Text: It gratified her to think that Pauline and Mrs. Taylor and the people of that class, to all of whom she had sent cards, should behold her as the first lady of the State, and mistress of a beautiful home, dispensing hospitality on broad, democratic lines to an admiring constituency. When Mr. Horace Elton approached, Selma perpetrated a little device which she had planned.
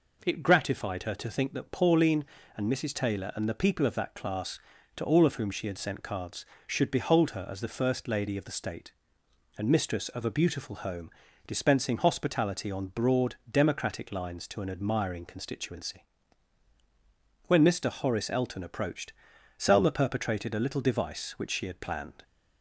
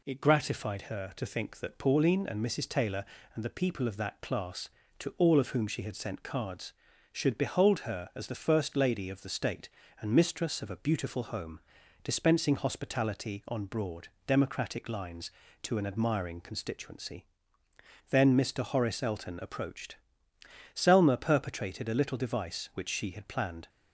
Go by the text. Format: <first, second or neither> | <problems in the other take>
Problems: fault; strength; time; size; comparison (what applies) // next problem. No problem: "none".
first | says "Then" for "When"; at 18.1 s